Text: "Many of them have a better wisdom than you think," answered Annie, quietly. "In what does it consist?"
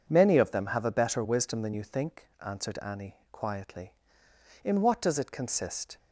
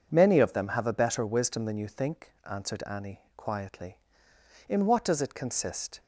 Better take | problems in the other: neither | none

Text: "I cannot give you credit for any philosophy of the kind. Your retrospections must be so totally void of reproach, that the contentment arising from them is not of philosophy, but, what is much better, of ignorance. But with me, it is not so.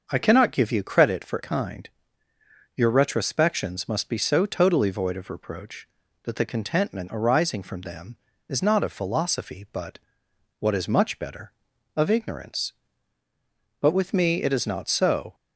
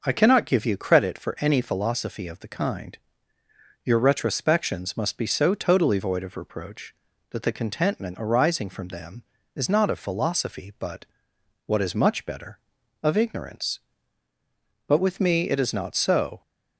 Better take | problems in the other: second | starts louder than the rest; until 1.1 s; 6.5 dB // skips "any philosophy of the"; at 1.4 s

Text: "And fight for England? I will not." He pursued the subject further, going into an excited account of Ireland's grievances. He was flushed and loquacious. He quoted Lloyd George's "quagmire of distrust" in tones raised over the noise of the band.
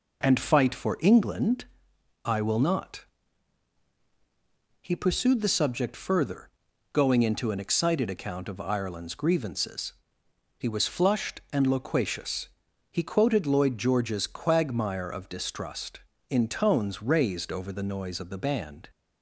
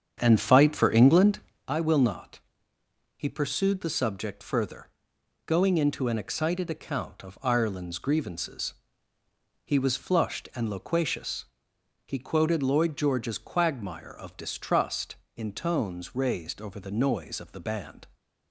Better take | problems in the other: first | starts louder than the rest; strong; until 1.7 s; 8 dB

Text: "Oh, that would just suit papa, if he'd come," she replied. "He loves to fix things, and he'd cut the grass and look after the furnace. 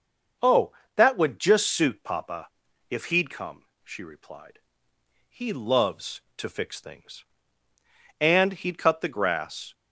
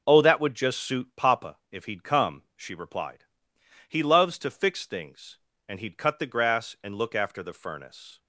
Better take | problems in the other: second | stops before "and look after the furnace"; at 9.7 s

